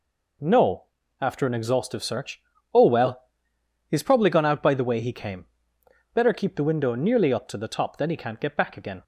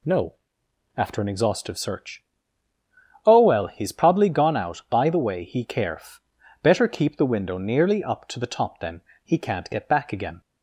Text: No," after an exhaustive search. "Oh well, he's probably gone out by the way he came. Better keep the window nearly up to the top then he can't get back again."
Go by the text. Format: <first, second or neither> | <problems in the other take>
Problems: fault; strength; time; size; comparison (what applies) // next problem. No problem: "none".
first | says "caref" for "came"; at 5.6 s // pauses between "then" and "he"; slight; at 9.0 s; 0.20 s long